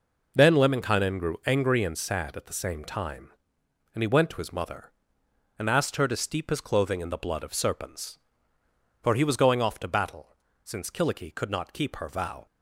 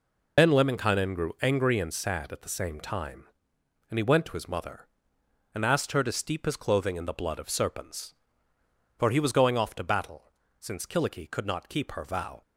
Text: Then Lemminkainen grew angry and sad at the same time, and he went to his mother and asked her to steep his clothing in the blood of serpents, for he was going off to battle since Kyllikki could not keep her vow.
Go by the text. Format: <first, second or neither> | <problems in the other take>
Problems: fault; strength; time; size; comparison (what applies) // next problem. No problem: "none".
first | loses the start of "Then"; at 0.3 s; 65 ms // pauses between "battle" and "since"; slight; at 10.3 s; 0.28 s long; slight in the first